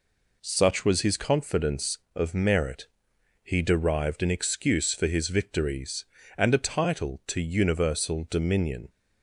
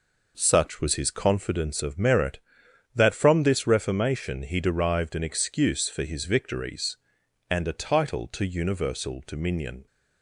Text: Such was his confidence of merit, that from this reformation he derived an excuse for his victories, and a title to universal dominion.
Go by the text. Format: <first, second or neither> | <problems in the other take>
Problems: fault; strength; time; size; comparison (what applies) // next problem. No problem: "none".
second | skips "that from this reformation"; at 3.1 s